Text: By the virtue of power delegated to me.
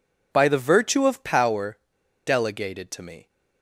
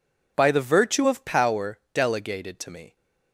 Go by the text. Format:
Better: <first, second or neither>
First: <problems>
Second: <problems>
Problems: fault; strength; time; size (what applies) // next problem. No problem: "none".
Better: second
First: pauses between "power" and "delegated"; noticeable; at 1.7 s; 0.49 s long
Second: none